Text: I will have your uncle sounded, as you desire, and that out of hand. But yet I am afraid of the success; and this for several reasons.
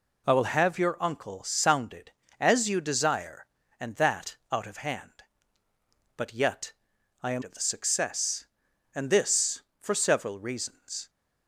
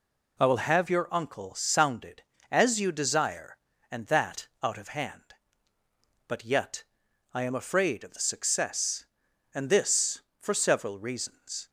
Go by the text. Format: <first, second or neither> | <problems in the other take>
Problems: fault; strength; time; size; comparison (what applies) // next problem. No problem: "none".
second | pauses between "yet" and "I"; noticeable; at 6.7 s; 0.50 s long; noticeable in the second // skips "afraid"; at 7.4 s